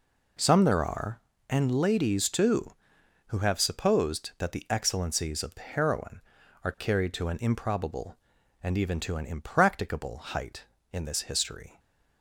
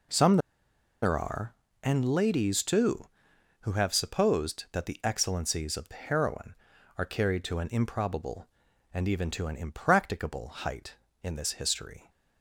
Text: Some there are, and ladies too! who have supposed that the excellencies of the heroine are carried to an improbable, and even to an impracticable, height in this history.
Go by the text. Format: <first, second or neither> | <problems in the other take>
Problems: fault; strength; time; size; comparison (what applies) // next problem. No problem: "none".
first | pauses between "Some" and "there"; noticeable; at 0.3 s; 0.64 s long